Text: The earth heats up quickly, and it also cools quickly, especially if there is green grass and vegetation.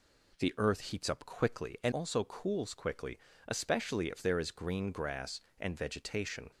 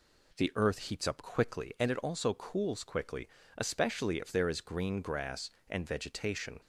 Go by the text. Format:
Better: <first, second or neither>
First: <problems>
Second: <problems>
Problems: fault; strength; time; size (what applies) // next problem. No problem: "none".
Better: second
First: skips "it"; at 1.9 s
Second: none